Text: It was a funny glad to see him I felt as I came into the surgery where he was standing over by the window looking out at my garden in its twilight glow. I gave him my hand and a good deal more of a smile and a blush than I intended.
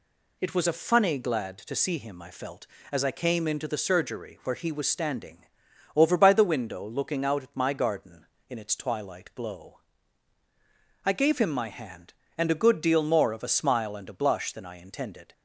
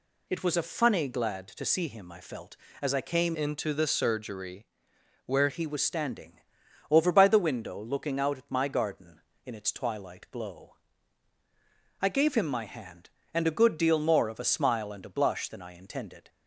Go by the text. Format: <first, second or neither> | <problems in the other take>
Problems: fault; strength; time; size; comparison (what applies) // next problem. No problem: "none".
first | changes voice from "into" to "where"; from 3.3 to 5.4 s; 2.1 s long // pauses between "surgery" and "where"; noticeable; at 4.6 s; 0.62 s long // pauses between "standing" and "over"; noticeable; at 6.3 s; 0.52 s long; noticeable in the first